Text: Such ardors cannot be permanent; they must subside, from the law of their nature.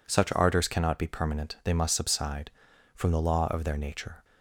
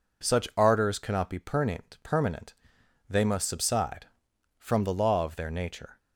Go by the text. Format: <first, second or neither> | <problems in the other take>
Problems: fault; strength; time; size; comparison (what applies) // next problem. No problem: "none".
first | says "permanent" twice; at 2.0 s